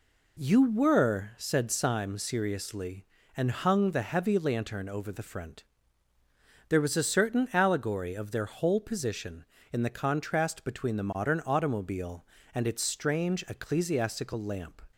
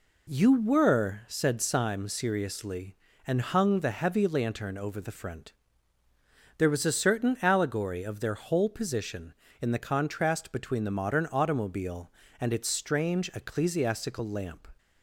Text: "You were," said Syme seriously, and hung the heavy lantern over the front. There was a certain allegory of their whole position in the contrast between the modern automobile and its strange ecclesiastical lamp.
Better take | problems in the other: neither | none

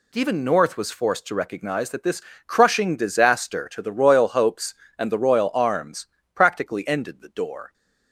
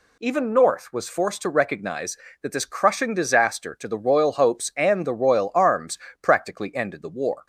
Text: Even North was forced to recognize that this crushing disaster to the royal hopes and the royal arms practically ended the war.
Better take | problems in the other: second | pauses between "this" and "crushing"; slight; at 2.2 s; 0.26 s long // pauses between "arms" and "practically"; slight; at 6.0 s; 0.26 s long; slight in the second // says "door" for "war"; at 7.2 s

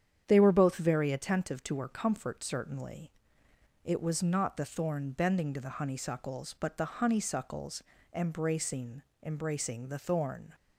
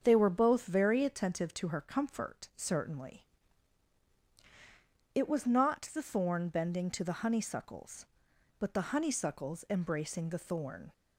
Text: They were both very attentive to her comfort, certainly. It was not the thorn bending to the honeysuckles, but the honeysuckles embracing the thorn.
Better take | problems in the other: second | starts louder than the rest; strong; until 1.2 s; 8.5 dB; strong in the second // pauses between "honeysuckles" and "embracing"; slight; at 7.8 s; 0.30 s long // says "embracing" twice; at 9.2 s

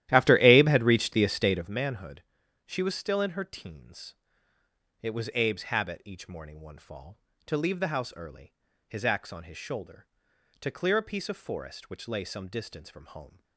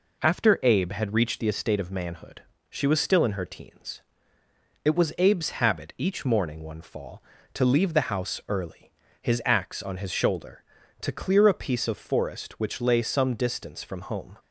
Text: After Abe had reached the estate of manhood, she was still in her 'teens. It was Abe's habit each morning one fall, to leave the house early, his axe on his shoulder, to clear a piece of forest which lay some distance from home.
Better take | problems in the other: second | starts louder than the rest; strong; until 1.7 s; 13 dB

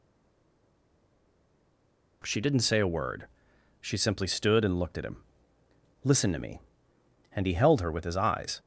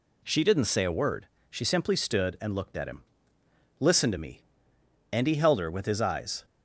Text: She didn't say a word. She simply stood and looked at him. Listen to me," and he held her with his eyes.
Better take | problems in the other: second | stays silent before the first word; until 2.2 s; 2.2 s long

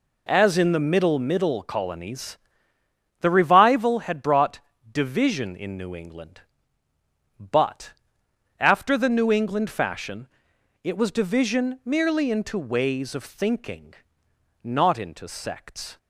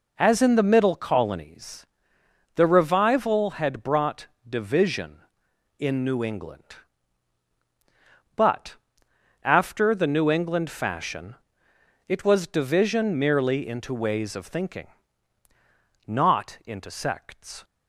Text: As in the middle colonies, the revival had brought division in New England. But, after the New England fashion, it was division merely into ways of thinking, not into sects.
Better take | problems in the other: second | says "middle" twice; at 1.1 s // pauses between "brought" and "division"; slight; at 4.5 s; 0.32 s long; slight in the second

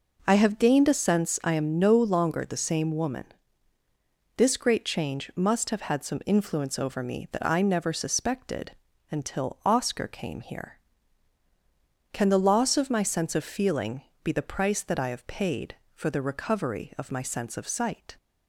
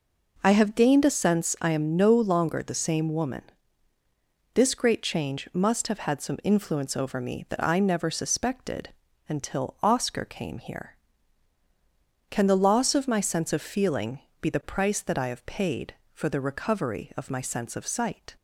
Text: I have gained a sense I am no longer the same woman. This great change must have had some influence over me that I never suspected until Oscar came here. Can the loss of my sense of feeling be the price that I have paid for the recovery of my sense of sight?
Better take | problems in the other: neither | pauses between "suspected" and "until"; the same in both // pauses between "feeling" and "be"; slight; the same in both

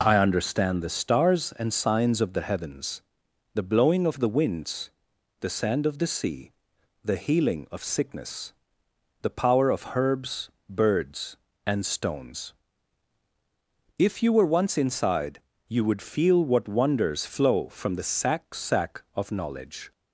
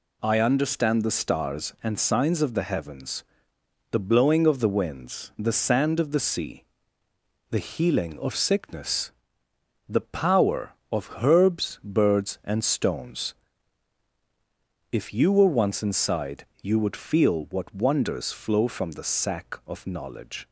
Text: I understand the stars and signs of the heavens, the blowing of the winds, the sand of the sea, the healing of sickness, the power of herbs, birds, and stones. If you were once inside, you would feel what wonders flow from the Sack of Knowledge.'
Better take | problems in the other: second | says "Sack" twice; at 18.5 s

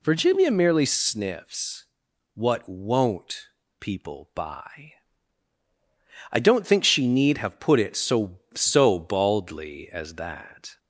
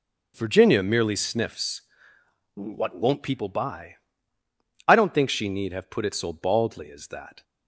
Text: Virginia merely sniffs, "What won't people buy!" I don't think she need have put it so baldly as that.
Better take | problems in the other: second | pauses between "won't" and "people"; slight; at 3.4 s; 0.32 s long // says "so" twice; at 8.5 s

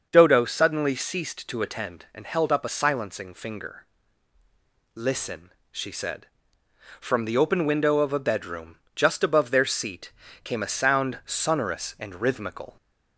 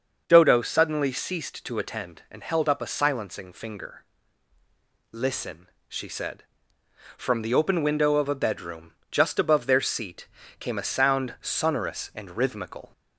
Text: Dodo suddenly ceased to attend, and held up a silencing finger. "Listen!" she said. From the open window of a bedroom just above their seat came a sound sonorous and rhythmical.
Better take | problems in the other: neither | starts louder than the rest; the same in both // pauses between "bedroom" and "just"; slight; the same in both // pauses between "seat" and "came"; slight; the same in both

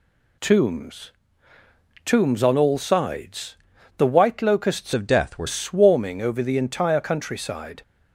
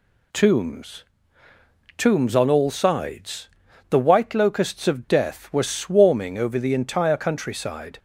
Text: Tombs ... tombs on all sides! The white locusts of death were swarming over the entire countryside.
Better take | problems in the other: second | changes voice from "of" to "were"; from 4.9 to 5.4 s; 0.5 s long

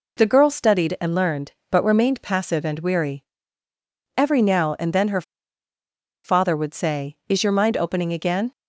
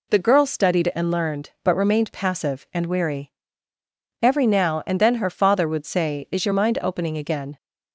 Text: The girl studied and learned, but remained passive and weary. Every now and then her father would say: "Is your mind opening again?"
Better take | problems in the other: second | pauses between "her" and "father"; at 5.2 s; 1.0 s long

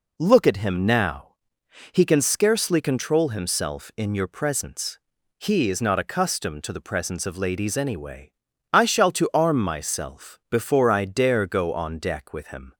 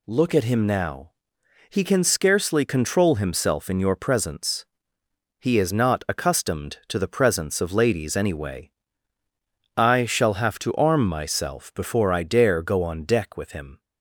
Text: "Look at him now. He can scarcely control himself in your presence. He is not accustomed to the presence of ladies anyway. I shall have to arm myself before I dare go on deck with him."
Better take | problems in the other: second | skips "have"; at 9.1 s

